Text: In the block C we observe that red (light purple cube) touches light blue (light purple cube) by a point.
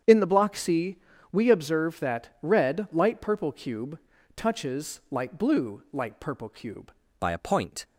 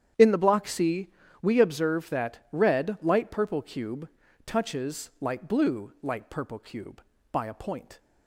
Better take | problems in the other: second | starts louder than the rest; strong; until 1.3 s; 8.5 dB; strong in the second // pauses between "C" and "we"; slight; at 0.9 s; 0.34 s long; slight in the second // changes voice at "by"; from 7.1 s on; 0.7 s long

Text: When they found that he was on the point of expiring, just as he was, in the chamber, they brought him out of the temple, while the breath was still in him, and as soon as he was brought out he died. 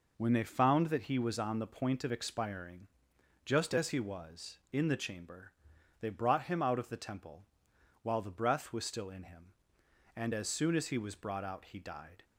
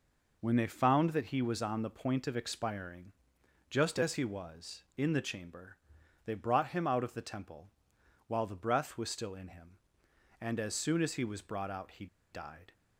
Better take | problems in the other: first | pauses between "he" and "died"; slight; at 12.0 s; 0.25 s long

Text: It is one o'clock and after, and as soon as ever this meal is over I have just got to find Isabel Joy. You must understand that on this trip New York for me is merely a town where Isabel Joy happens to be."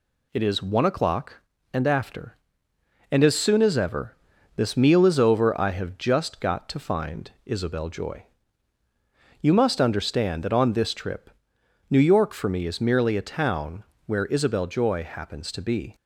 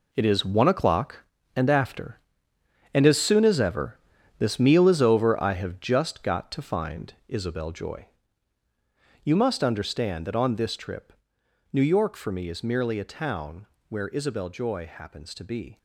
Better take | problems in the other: first | gets quieter; strong; throughout; 10.5 dB // pauses between "ever" and "this"; at 3.9 s; 0.42 s long; also in the first // pauses between "find" and "Isabel"; slight; at 7.1 s; 0.16 s long; slight in the first // pauses between "trip" and "New"; noticeable; at 11.1 s; 0.58 s long; noticeable in the first // pauses between "town" and "where"; slight; at 13.6 s; 0.20 s long; slight in the first

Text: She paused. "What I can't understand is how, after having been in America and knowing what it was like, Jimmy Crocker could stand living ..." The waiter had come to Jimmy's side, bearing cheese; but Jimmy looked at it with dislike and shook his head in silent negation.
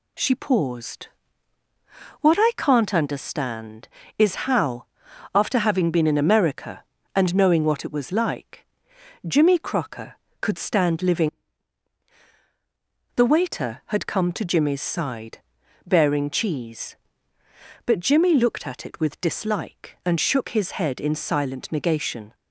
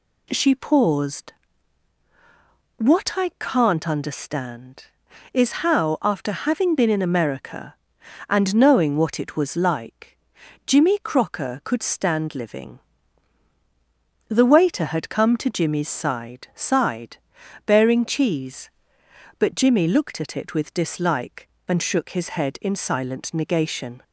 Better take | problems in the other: first | says "side" twice; at 16.5 s

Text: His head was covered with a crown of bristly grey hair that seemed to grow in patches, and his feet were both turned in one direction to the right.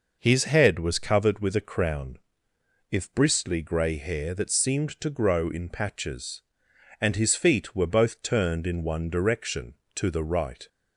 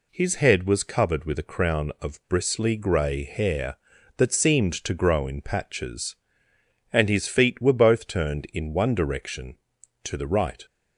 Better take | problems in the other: second | says "if" for "of"; at 2.9 s

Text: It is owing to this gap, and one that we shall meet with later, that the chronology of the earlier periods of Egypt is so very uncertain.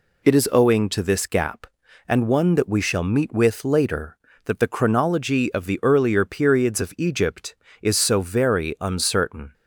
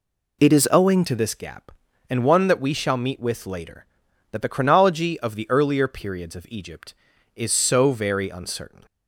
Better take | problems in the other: first | changes voice at "to"; from 1.0 s on; 7.8 s long

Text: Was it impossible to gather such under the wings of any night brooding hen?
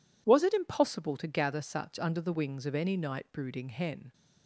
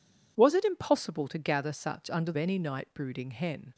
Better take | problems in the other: first | skips "the wings of"; at 2.3 s

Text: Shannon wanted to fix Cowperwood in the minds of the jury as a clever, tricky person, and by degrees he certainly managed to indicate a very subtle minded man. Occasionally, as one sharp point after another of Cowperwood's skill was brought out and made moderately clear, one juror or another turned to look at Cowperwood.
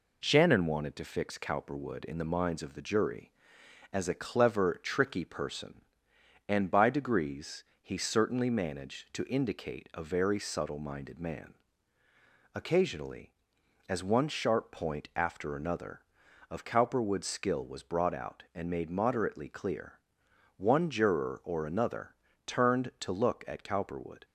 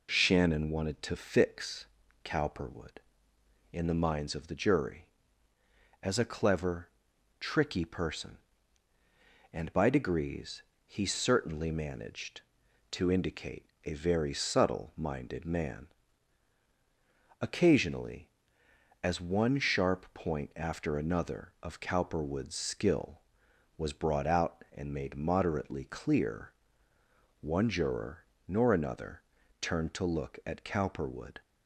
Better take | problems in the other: first | pauses between "fix" and "Cowperwood"; at 1.8 s; 0.38 s long // pauses between "degrees" and "he"; slight; at 10.6 s; 0.24 s long; slight in the first // pauses between "indicate" and "a"; slight; at 13.6 s; 0.20 s long // says "nor" for "or"; at 28.4 s // pauses between "another" and "turned"; at 29.2 s; 0.40 s long; slight in the first

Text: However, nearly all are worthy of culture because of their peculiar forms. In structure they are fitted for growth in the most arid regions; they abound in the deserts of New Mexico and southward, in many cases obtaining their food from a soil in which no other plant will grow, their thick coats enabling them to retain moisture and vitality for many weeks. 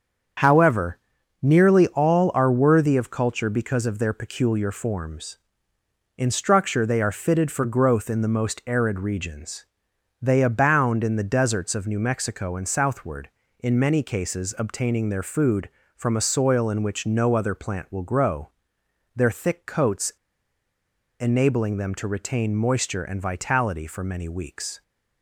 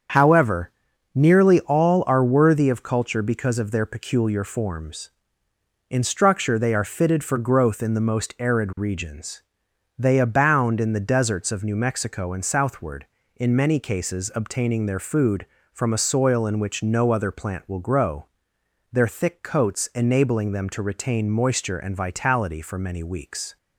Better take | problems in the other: second | starts louder than the rest; strong; until 1.7 s; 7 dB; strong in the second // pauses between "coats" and "enabling"; at 20.1 s; 1.0 s long

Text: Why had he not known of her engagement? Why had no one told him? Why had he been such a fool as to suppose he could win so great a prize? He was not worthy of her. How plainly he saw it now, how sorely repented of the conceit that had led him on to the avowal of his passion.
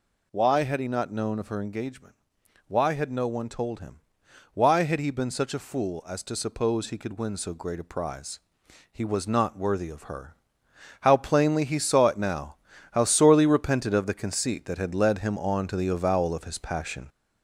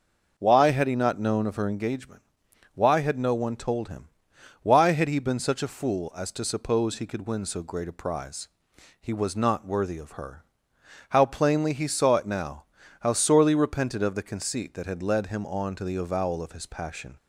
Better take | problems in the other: second | gets louder; throughout; 4 dB

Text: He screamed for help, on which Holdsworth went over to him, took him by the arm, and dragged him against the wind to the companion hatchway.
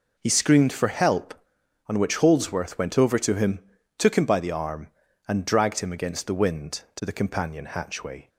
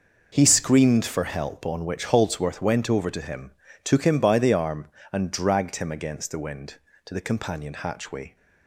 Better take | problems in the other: neither | none

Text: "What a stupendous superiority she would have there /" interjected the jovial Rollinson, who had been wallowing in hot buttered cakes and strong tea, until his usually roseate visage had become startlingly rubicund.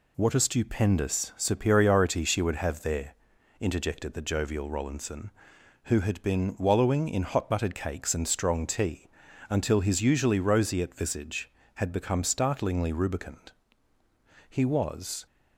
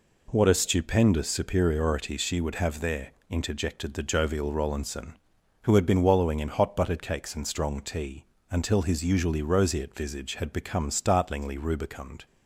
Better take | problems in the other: second | goes on to say "He was"; noticeable; from 14.4 s on; 0.76 s long

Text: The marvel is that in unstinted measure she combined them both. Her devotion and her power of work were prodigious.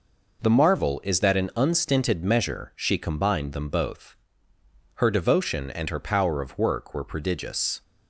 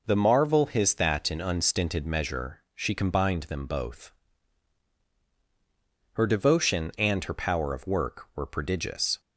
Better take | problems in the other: first | says "his" for "is"; at 0.6 s

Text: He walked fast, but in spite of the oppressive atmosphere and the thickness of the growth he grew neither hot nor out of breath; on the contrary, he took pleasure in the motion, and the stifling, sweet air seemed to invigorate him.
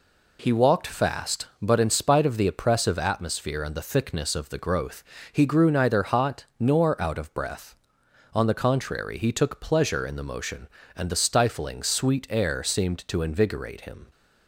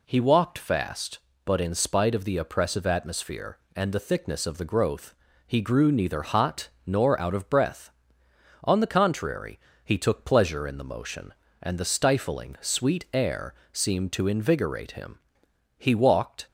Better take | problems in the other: first | pauses between "growth" and "he"; slight; at 5.1 s; 0.34 s long; slight in the first // pauses between "hot" and "nor"; slight; at 6.6 s; 0.18 s long // pauses between "air" and "seemed"; slight; at 13.5 s; 0.20 s long // goes on to say "He walked"; noticeable; from 15.7 s on; 0.70 s long

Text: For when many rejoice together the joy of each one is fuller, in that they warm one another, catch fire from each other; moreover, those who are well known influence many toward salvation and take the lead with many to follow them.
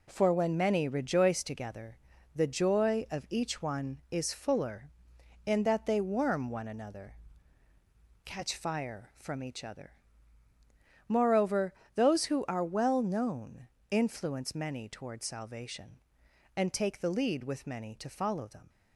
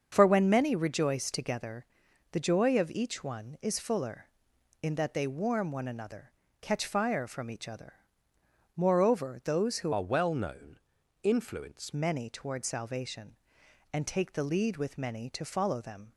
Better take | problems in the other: first | starts louder than the rest; until 1.1 s; 6.5 dB // pauses between "together" and "the"; noticeable; at 1.8 s; 0.46 s long; also in the first // changes voice from "are" to "influence"; from 9.9 to 11.9 s; 2.0 s long // pauses between "known" and "influence"; at 10.7 s; 0.42 s long; slight in the first

